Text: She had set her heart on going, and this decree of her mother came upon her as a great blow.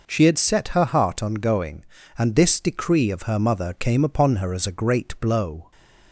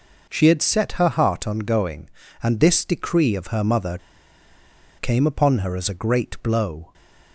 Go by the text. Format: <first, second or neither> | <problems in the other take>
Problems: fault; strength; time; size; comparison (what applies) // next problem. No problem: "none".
first | pauses between "mother" and "came"; at 3.9 s; 1.0 s long // stays silent after the last word; slight; from 6.8 s on; 0.5 s long; slight in the first